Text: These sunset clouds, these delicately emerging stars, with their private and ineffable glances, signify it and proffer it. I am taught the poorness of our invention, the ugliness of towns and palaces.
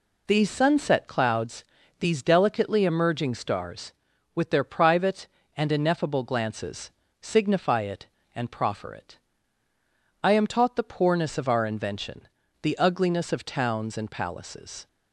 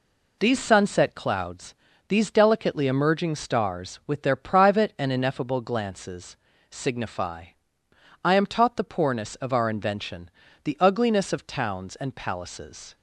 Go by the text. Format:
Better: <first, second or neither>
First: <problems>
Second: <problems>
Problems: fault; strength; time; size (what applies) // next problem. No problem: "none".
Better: first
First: none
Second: skips "it and proffer it"; at 7.8 s